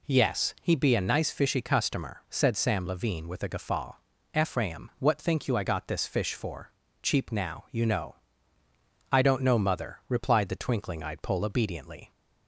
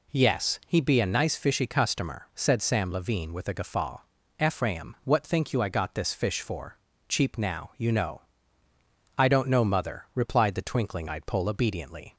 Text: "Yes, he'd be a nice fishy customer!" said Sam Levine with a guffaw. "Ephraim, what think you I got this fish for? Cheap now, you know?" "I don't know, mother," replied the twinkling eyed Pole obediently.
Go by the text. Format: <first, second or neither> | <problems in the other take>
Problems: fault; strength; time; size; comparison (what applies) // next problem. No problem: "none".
neither | none